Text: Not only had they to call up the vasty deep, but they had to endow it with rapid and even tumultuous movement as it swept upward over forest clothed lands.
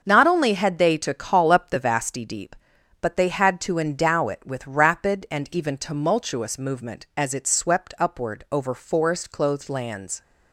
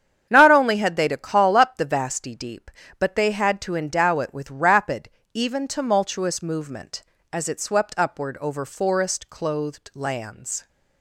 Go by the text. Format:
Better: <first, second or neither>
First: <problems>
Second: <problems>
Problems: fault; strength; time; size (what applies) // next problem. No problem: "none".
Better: first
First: starts louder than the rest; until 1.0 s; 6.5 dB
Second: starts louder than the rest; strong; until 1.3 s; 8.5 dB // skips "and"; at 5.2 s